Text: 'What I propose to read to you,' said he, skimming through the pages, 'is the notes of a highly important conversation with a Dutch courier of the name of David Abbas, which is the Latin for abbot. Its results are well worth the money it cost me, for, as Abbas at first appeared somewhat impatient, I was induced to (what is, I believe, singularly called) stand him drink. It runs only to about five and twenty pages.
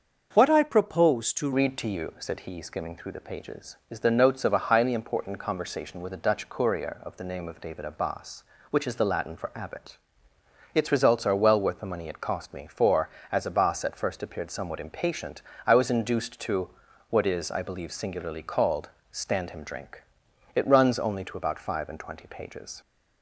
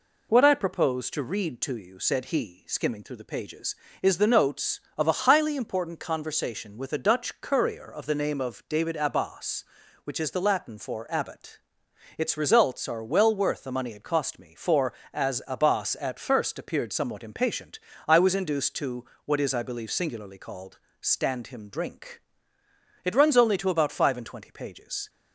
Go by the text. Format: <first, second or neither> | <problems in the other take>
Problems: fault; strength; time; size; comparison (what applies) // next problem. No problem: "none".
second | starts louder than the rest; until 1.3 s; 6.5 dB // changes voice at "read"; from 1.5 s on; 21.3 s long